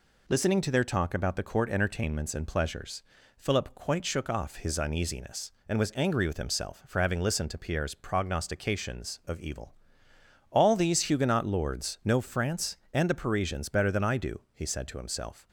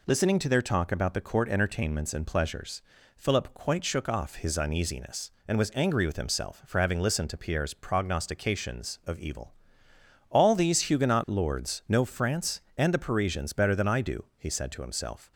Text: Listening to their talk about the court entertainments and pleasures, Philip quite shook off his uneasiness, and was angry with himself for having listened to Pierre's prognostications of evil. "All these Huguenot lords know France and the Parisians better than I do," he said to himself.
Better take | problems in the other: neither | none

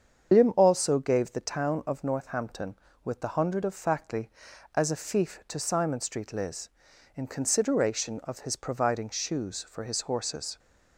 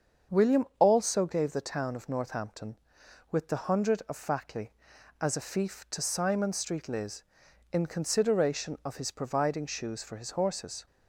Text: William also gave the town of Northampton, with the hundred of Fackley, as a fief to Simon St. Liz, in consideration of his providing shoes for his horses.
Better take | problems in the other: second | loses the start of "William"; at 0.3 s; 170 ms // starts louder than the rest; strong; until 1.3 s; 7.5 dB; also in the second

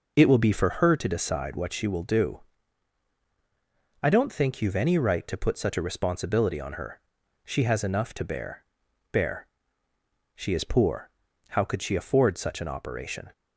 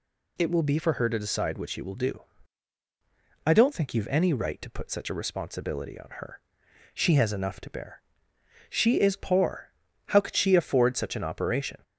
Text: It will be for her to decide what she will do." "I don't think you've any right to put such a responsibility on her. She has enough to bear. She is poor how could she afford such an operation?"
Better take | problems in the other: second | says "bear" twice; at 9.1 s // pauses between "poor" and "how"; at 11.1 s; 0.38 s long; also in the second

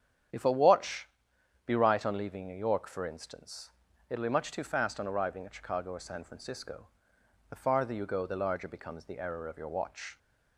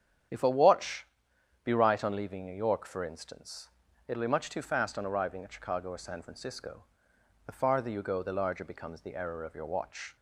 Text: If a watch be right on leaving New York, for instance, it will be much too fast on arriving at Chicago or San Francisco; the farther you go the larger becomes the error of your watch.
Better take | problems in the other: neither | starts louder than the rest; strong; the same in both // pauses between "watch" and "be"; noticeable; the same in both

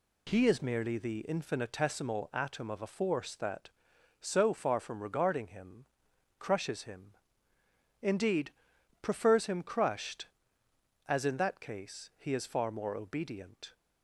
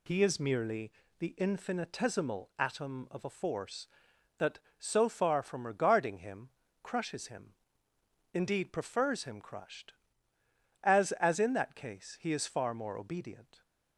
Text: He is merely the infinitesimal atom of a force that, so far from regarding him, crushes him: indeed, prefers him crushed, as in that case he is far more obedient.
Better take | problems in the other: first | pauses between "merely" and "the"; slight; at 0.8 s; 0.30 s long // says "as" twice; at 11.1 s

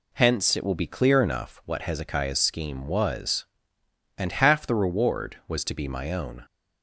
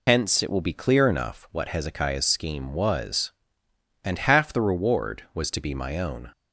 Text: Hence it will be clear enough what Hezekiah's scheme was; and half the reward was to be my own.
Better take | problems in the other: first | loses the start of "Hence"; at 0.0 s; 70 ms

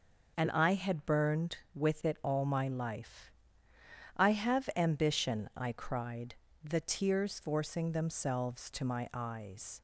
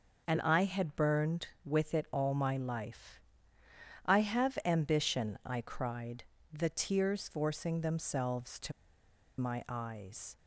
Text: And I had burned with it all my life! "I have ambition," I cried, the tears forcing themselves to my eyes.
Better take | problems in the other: first | pauses between "to" and "my"; noticeable; at 8.7 s; 0.68 s long

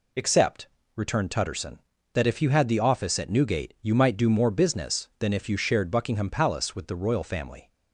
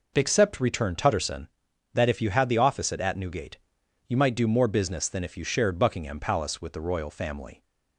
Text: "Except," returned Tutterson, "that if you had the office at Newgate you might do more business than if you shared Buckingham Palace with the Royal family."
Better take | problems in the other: first | says "at" twice; at 2.9 s // pauses between "Newgate" and "you"; noticeable; at 3.5 s; 0.50 s long

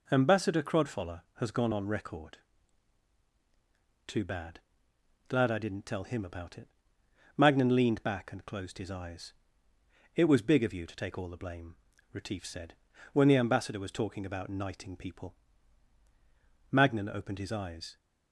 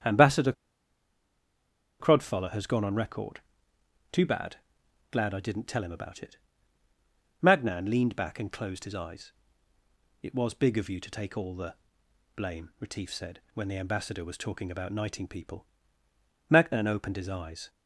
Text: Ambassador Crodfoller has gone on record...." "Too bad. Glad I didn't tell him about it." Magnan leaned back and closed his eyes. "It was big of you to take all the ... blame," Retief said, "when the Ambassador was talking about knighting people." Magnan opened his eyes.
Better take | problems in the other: first | starts louder than the rest; strong; until 2.5 s; 8.5 dB // pauses between "Ambassador" and "Crodfoller"; strong; at 0.5 s; 1.4 s long

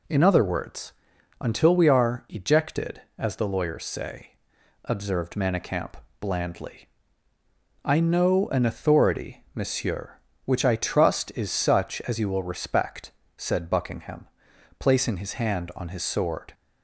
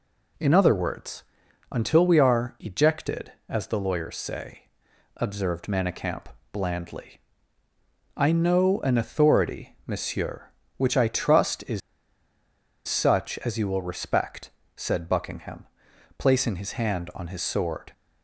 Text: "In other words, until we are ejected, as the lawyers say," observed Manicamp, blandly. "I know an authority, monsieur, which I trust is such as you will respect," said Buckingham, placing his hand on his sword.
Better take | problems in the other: first | pauses between "is" and "such"; at 11.8 s; 1.0 s long

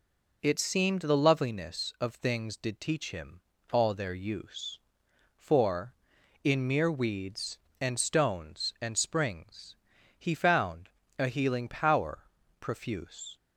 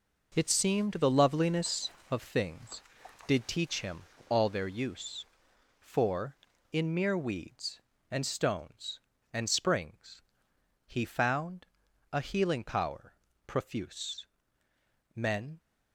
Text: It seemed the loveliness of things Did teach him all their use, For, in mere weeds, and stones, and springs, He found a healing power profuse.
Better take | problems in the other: first | pauses between "him" and "all"; slight; at 4.0 s; 0.26 s long; slight in the first // pauses between "found" and "a"; at 11.6 s; 0.44 s long; slight in the first // pauses between "power" and "profuse"; slight; at 13.1 s; 0.32 s long; also in the first // goes on to say "Men"; slight; from 15.1 s on; 0.44 s long

